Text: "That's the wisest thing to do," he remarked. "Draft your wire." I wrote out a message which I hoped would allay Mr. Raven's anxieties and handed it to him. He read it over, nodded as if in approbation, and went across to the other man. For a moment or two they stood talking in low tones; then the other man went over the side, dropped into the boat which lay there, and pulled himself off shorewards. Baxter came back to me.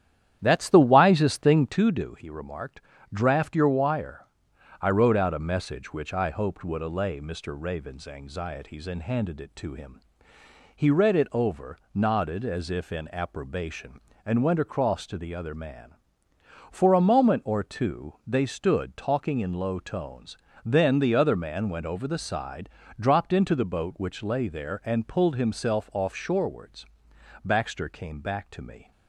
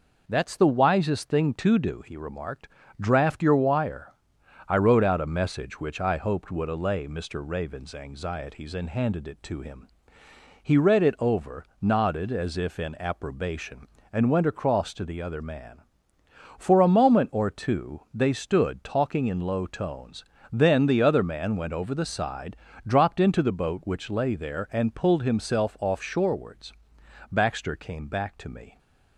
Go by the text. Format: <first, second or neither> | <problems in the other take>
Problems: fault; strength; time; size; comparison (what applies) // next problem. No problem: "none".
second | starts louder than the rest; strong; until 1.8 s; 10.5 dB